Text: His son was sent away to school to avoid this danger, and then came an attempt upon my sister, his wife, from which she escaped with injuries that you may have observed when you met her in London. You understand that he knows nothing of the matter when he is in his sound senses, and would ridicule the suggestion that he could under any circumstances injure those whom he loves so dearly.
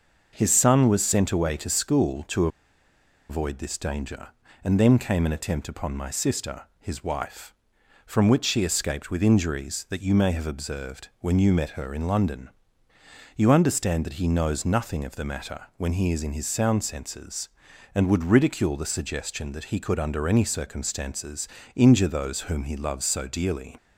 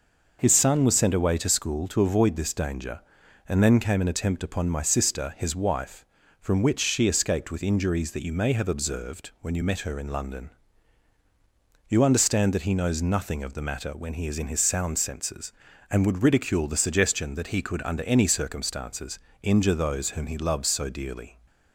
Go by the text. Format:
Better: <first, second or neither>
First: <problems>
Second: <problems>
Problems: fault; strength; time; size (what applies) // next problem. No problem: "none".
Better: second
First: pauses between "to" and "avoid"; noticeable; at 2.4 s; 0.81 s long // pauses between "circumstances" and "injure"; slight; at 21.4 s; 0.28 s long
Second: pauses between "circumstances" and "injure"; slight; at 19.1 s; 0.24 s long